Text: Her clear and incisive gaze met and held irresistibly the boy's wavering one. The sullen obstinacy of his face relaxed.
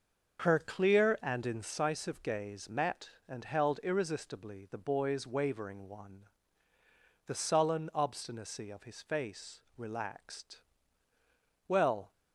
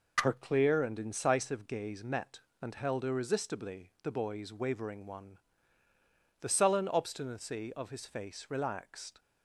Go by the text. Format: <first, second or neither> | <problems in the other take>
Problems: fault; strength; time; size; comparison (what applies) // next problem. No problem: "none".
second | starts louder than the rest; until 1.4 s; 6.5 dB // pauses between "face" and "relaxed"; slight; at 9.6 s; 0.16 s long // goes on to say "Well"; slight; from 11.6 s on; 0.44 s long